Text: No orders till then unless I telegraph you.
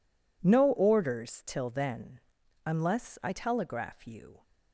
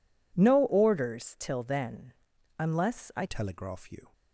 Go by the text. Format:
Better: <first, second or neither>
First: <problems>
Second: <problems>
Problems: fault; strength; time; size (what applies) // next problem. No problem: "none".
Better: first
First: pauses between "then" and "unless"; noticeable; at 2.1 s; 0.46 s long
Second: pauses between "then" and "unless"; noticeable; at 2.1 s; 0.46 s long // changes voice at "telegraph"; from 3.2 s on; 0.9 s long